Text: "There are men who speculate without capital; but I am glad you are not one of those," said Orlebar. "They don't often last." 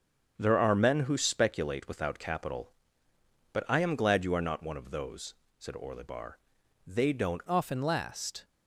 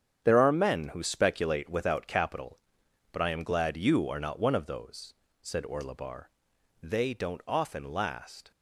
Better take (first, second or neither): second